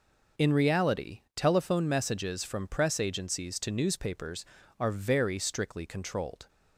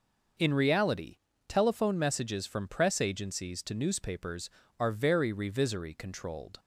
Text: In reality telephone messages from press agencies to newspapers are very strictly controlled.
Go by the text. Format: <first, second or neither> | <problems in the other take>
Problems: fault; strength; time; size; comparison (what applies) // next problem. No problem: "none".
first | pauses between "reality" and "telephone"; slight; at 1.1 s; 0.32 s long; slight in the first // says "revisory" for "strictly"; at 5.3 s